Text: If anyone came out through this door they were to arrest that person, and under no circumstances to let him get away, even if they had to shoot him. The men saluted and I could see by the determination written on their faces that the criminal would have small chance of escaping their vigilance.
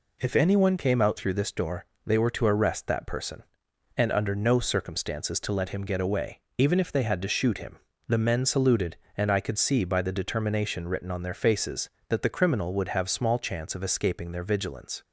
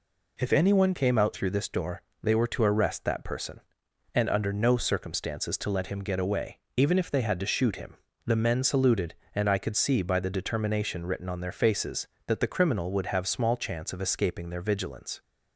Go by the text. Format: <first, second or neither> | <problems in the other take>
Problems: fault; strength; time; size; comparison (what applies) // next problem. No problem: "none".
neither | pauses between "door" and "they"; slight; the same in both